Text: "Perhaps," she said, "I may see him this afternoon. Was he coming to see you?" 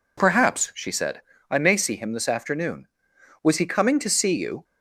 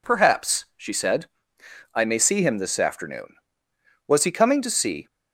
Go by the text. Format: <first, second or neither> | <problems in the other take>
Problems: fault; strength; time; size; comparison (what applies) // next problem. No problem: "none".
first | stops before "you"; at 5.0 s